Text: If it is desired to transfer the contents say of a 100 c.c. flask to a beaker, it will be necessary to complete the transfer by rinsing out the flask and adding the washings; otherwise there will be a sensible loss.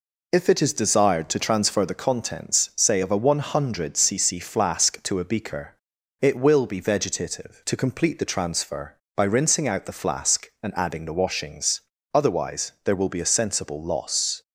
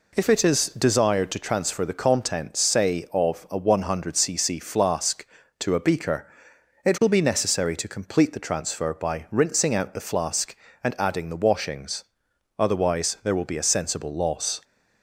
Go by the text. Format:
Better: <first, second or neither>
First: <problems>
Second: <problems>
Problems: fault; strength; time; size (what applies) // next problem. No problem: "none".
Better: second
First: says "vegetative" for "necessary"; at 6.8 s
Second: none